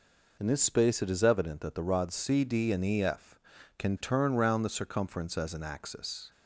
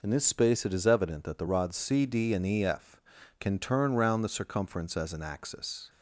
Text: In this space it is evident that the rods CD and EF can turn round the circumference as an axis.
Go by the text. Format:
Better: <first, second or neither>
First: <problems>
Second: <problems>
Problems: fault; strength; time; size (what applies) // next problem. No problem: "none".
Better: neither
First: none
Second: none